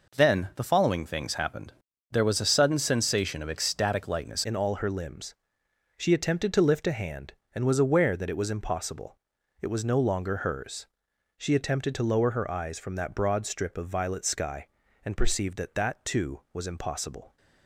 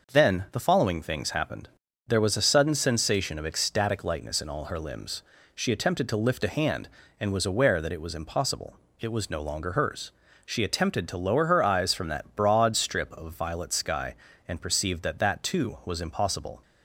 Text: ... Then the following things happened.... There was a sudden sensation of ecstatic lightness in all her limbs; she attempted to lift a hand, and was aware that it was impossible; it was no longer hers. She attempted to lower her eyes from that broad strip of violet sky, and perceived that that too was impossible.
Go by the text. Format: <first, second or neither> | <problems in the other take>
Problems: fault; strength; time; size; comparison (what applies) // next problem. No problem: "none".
second | changes voice at "in"; from 4.4 s on; 12.9 s long